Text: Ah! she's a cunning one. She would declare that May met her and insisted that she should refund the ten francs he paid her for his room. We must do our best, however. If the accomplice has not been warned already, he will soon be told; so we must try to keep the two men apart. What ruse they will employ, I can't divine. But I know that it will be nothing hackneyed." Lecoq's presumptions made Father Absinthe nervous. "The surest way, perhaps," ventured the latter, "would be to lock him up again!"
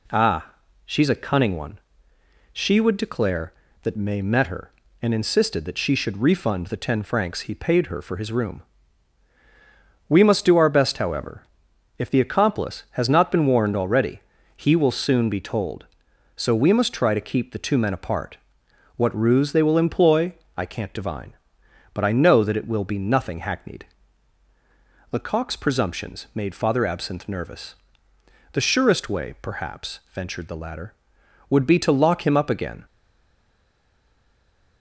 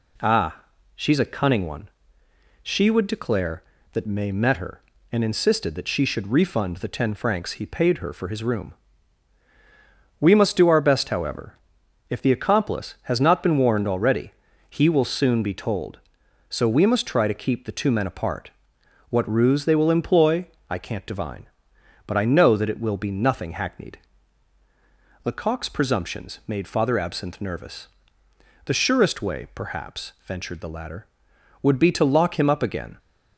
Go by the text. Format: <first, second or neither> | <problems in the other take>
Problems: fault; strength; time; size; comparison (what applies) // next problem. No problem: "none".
second | stays silent after the last word; noticeable; from 32.8 s on; 2.0 s long